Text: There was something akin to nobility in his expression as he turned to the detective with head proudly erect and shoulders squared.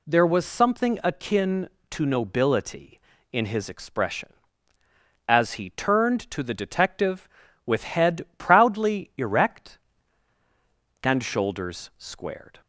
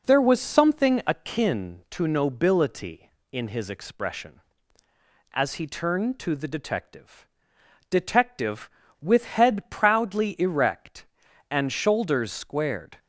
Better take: first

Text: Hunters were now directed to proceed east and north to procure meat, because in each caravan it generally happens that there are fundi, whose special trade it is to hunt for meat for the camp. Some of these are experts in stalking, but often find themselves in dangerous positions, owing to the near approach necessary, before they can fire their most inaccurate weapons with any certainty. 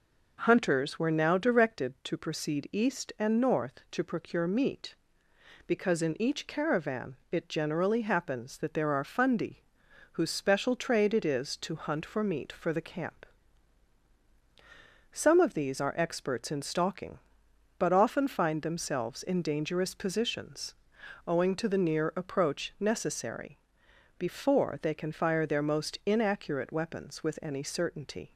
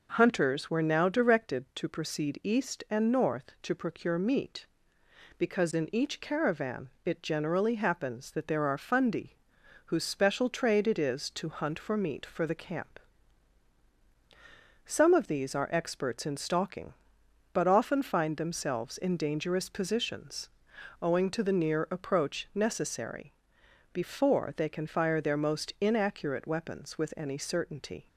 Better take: neither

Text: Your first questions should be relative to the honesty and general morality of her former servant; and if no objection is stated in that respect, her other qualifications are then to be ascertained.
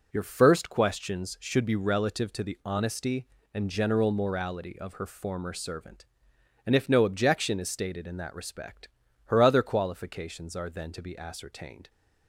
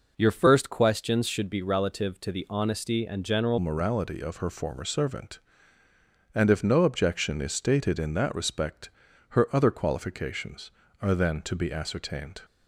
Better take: first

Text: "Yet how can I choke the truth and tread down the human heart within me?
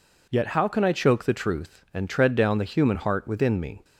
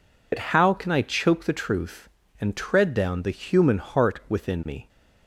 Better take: first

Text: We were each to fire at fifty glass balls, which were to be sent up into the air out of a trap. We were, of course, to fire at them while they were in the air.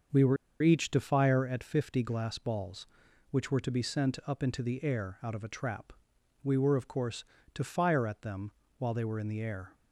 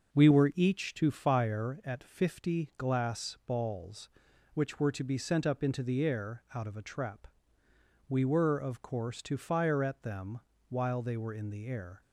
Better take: second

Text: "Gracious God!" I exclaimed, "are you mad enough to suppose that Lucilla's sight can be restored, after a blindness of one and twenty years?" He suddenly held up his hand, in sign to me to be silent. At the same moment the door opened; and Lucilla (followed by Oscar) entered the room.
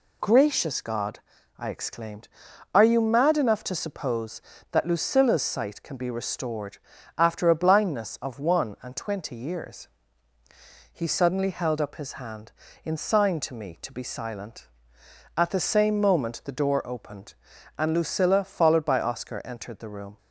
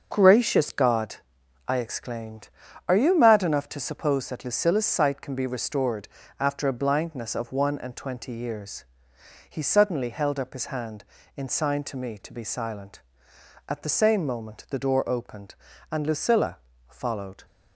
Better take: first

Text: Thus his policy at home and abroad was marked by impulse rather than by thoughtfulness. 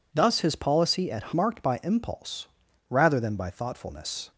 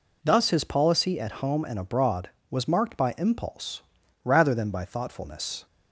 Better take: second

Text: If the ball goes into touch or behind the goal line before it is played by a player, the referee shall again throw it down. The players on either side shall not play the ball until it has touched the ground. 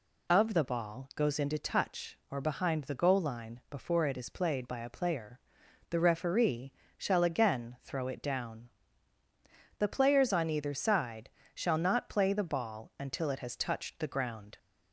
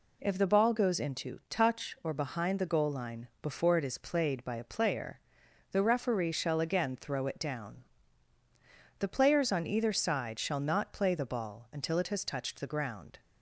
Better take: second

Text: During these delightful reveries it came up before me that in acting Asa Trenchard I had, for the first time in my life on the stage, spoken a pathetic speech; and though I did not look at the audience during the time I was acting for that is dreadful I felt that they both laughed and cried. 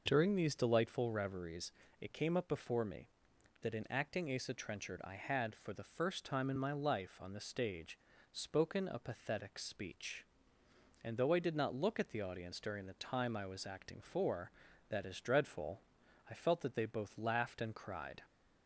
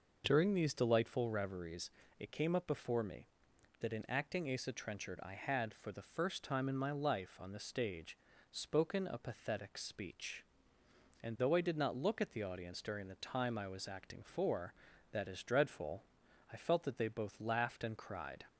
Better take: neither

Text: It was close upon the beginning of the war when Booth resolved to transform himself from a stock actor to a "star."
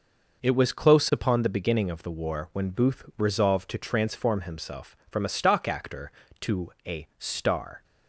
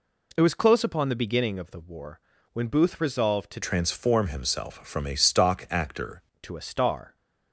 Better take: first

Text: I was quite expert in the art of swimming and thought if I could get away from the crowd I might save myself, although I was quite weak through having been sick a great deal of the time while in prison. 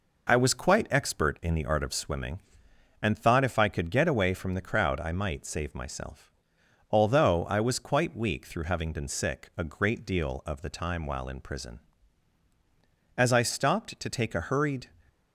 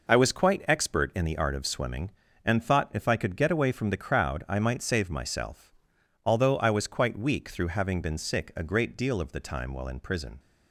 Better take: second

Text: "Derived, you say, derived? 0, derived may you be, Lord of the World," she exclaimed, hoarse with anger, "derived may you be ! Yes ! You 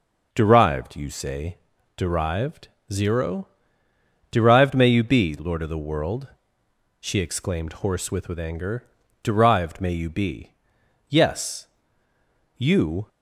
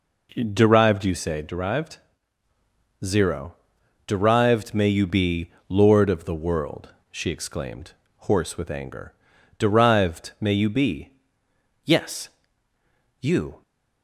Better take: second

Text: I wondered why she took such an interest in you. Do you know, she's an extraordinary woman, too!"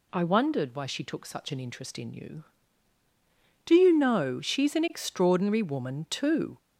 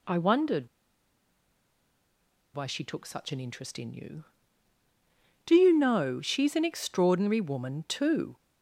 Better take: first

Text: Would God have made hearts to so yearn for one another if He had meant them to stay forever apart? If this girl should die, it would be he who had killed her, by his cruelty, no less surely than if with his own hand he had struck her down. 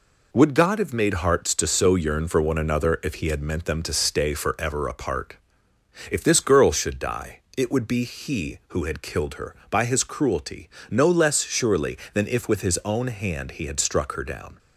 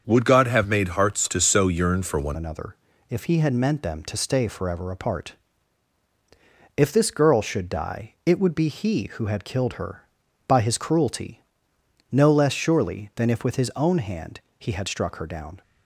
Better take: first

